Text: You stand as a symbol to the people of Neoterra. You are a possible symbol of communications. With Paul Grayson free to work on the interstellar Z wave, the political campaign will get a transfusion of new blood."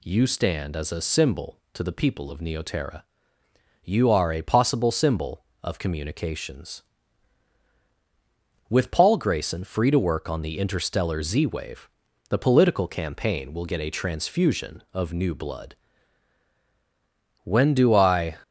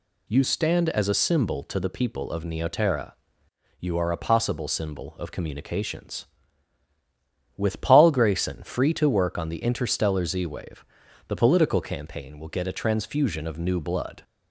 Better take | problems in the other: second | goes on to say "When do I"; noticeable; from 17.4 s on; 0.94 s long

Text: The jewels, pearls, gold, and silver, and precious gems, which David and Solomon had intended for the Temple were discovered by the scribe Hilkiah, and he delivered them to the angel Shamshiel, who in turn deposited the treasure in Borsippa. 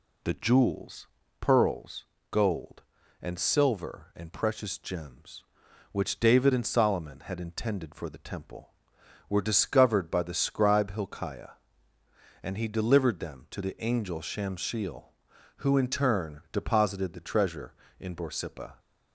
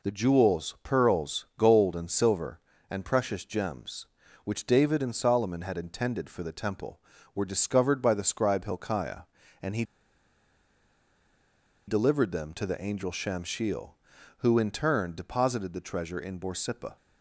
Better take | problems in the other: first | pauses between "he" and "delivered"; strong; at 9.8 s; 2.0 s long

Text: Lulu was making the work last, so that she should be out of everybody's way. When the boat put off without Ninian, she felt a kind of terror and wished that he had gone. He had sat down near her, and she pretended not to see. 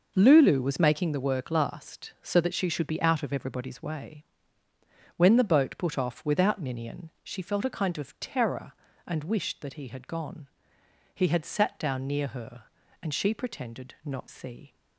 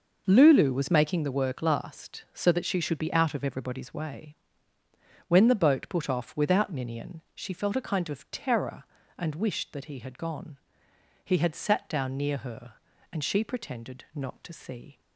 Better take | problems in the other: second | skips "to"; at 14.2 s

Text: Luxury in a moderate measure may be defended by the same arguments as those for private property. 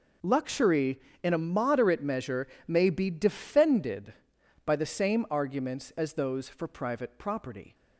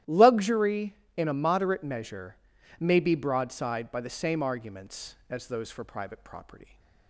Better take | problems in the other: first | starts louder than the rest; strong; until 1.2 s; 13 dB // pauses between "measure" and "may"; noticeable; at 2.3 s; 0.46 s long; slight in the first // says "broadside" for "defended"; at 3.1 s

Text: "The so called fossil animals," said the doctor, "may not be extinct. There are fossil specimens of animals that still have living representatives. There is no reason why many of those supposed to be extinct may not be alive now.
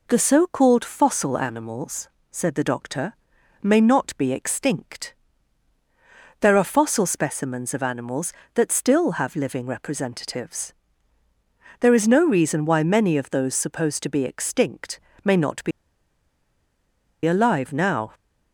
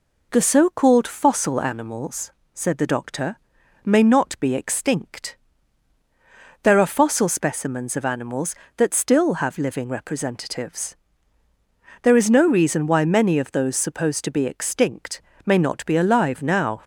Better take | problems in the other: second | pauses between "extinct" and "may"; slight; at 14.9 s; 0.24 s long; slight in the second // pauses between "be" and "alive"; strong; at 15.7 s; 1.5 s long

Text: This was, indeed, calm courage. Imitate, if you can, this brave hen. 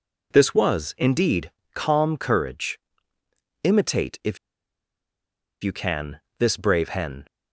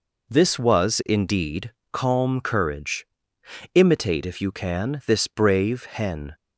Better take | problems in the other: second | pauses between "if" and "you"; strong; at 4.3 s; 1.2 s long

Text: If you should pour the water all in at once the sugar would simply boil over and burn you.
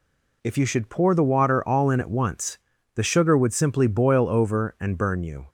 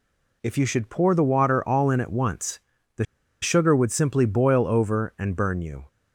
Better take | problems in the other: first | pauses between "once" and "the"; slight; at 2.5 s; 0.36 s long; slight in the first // pauses between "the" and "sugar"; at 3.0 s; 0.38 s long

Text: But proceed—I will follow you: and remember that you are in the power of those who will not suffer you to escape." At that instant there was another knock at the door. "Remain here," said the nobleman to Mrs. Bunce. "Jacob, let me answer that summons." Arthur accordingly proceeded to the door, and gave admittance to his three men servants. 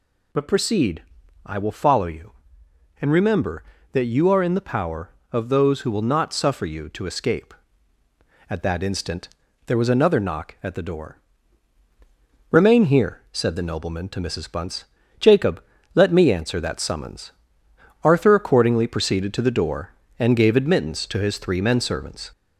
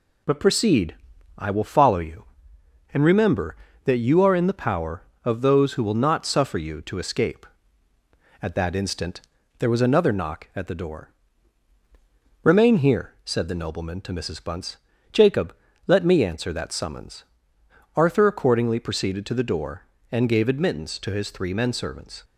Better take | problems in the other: second | gets louder; slight; throughout; 2 dB // pauses between "instant" and "there"; slight; at 9.2 s; 0.36 s long; slight in the second

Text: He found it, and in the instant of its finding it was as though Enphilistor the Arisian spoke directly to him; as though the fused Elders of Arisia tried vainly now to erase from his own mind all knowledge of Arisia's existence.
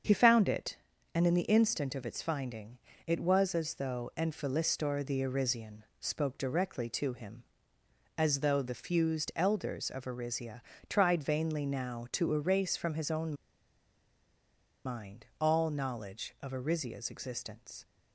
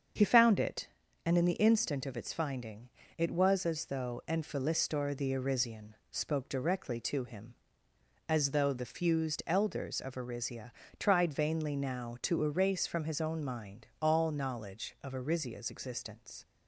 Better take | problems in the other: second | starts louder than the rest; until 1.4 s; 7 dB; also in the second // pauses between "finding" and "it"; slight; at 2.7 s; 0.30 s long; slight in the second // pauses between "Arisian" and "spoke"; slight; at 5.8 s; 0.16 s long; slight in the second // pauses between "Arisia" and "tried"; slight; at 10.6 s; 0.26 s long; slight in the second // pauses between "own" and "mind"; strong; at 13.3 s; 1.5 s long

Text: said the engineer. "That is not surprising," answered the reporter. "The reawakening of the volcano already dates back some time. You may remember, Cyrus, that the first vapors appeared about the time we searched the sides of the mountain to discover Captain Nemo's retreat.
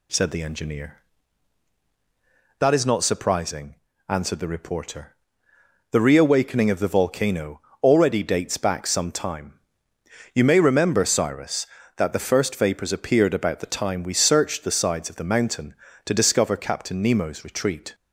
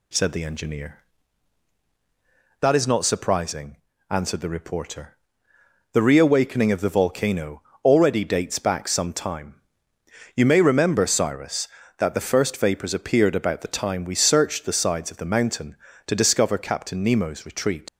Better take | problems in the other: first | pauses between "volcano" and "already"; slight; at 7.6 s; 0.22 s long; slight in the first // leaves "retreat" unfinished; at 17.8 s; 75 ms

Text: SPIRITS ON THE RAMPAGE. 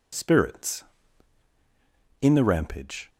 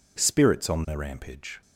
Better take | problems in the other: second | says "In" for "ON"; at 2.2 s

